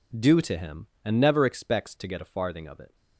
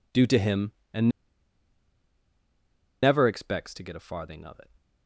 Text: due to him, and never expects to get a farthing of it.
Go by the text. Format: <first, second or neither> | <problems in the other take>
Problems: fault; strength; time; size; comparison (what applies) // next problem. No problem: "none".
first | pauses between "and" and "never"; strong; at 1.0 s; 1.9 s long